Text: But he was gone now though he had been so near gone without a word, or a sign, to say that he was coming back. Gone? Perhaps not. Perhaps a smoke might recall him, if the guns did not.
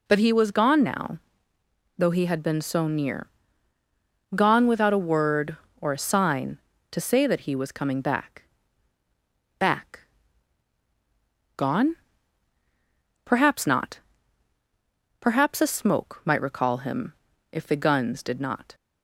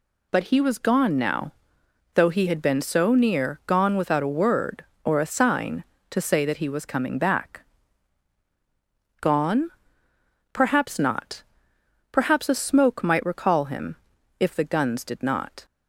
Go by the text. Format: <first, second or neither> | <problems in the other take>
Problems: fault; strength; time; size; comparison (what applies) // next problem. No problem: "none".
second | pauses between "now" and "though"; noticeable; at 1.1 s; 0.78 s long; noticeable in the second // pauses between "near" and "gone"; at 3.2 s; 1.0 s long // says "back" twice; at 9.5 s